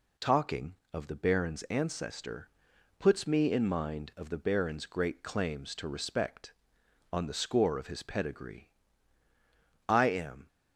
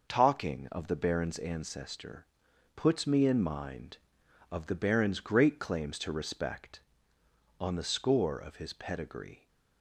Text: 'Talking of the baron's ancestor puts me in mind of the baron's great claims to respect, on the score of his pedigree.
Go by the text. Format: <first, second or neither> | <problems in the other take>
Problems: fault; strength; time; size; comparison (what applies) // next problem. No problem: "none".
second | pauses between "ancestor" and "puts"; noticeable; at 2.4 s; 0.50 s long; noticeable in the second // goes on to say "I am"; from 9.8 s on; 0.60 s long